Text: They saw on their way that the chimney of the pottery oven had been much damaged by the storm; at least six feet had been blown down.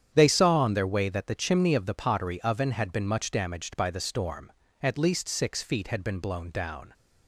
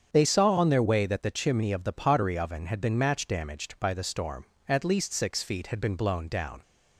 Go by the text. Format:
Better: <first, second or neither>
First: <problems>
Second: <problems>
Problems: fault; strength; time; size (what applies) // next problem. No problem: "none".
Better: first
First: starts louder than the rest; strong; until 1.1 s; 9 dB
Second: starts louder than the rest; strong; until 1.1 s; 7.5 dB // says "match" for "much"; at 2.9 s